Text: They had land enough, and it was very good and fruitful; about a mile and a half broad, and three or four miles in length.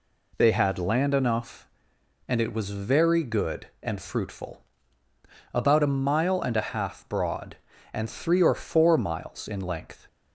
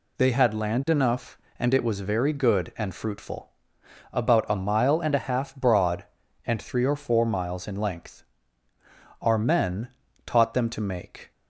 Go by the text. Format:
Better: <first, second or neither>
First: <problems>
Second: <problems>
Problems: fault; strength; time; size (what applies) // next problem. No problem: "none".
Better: first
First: none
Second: goes on to say "Our men taught them to make"; strong; from 9.2 s on; 2.1 s long